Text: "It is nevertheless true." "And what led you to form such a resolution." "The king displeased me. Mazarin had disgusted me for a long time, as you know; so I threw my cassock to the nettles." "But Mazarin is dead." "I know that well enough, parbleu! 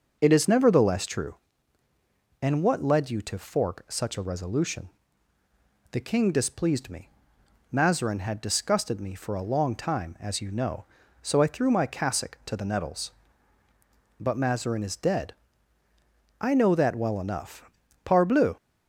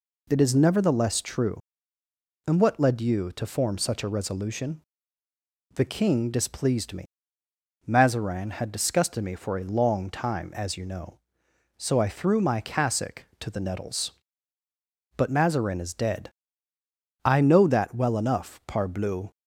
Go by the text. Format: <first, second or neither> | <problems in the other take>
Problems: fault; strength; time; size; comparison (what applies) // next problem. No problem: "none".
second | starts louder than the rest; until 1.2 s; 6.5 dB // says "fork" for "form"; at 3.3 s